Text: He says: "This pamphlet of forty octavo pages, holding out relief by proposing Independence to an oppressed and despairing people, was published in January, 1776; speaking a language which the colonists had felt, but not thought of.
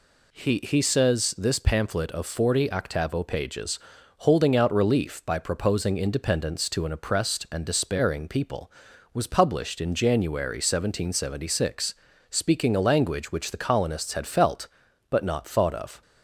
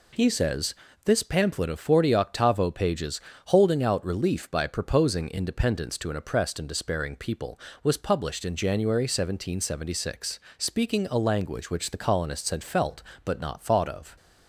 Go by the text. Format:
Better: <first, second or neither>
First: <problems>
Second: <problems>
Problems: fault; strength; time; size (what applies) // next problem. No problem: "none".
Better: second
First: says "He" twice; at 0.6 s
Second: none